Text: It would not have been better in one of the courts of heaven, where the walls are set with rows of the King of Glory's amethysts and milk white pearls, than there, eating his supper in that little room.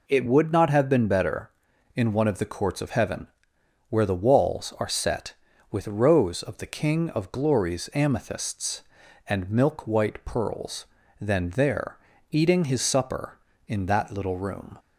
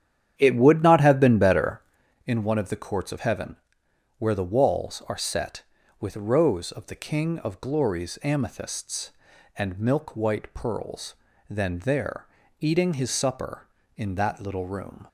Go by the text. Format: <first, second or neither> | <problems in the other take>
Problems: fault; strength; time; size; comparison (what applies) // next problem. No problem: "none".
first | starts louder than the rest; strong; until 2.2 s; 9.5 dB